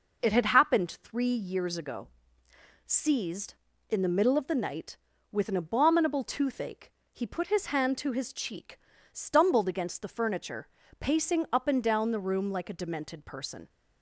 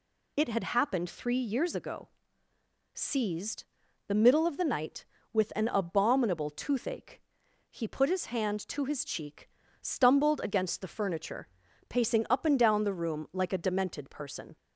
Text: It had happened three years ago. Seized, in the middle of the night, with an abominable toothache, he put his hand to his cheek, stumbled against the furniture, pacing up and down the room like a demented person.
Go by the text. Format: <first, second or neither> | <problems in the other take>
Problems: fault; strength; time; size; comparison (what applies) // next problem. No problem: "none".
first | skips "in"; at 3.8 s